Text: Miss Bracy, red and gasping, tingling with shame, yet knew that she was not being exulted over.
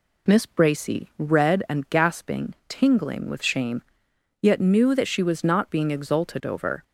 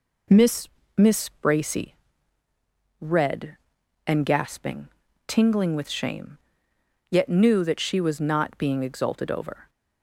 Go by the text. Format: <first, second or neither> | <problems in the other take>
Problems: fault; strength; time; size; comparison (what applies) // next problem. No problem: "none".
first | says "Miss" twice; at 0.9 s